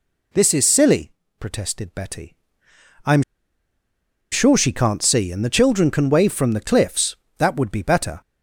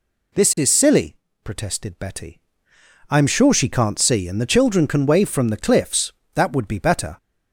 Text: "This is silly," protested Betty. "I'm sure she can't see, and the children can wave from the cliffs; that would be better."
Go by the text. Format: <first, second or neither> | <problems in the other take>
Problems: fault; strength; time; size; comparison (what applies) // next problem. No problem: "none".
second | pauses between "I'm" and "sure"; at 3.2 s; 1.1 s long